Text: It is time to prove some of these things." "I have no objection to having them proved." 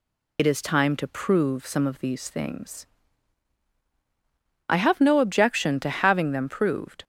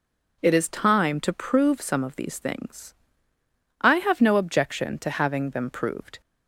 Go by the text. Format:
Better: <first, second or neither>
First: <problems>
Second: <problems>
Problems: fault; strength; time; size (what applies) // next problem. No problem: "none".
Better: second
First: loses the start of "It"; at 0.3 s; 65 ms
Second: none